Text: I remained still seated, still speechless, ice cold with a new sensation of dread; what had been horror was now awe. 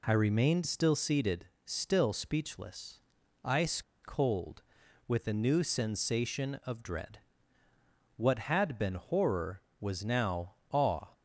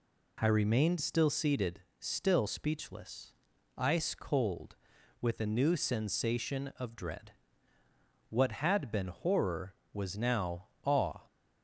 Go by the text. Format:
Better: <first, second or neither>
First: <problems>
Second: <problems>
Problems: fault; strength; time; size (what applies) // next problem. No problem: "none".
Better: second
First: pauses between "ice" and "cold"; slight; at 3.8 s; 0.22 s long // pauses between "now" and "awe"; slight; at 10.5 s; 0.18 s long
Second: pauses between "now" and "awe"; slight; at 10.6 s; 0.18 s long